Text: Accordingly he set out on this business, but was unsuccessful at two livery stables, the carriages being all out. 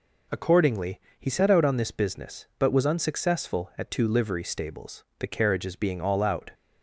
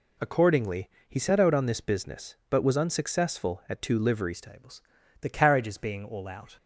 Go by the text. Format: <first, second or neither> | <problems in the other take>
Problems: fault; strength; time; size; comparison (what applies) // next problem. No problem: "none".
first | pauses between "Accordingly" and "he"; slight; at 0.8 s; 0.18 s long; slight in the first // changes voice at "stables"; from 4.3 s on; 2.2 s long